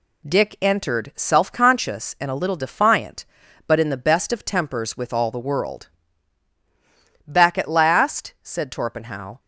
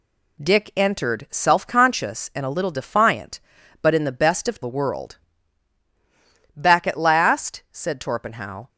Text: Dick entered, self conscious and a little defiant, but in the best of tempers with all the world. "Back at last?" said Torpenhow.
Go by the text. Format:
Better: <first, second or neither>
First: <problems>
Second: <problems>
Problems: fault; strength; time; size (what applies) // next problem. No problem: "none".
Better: first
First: none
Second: skips "tempers with all"; at 4.6 s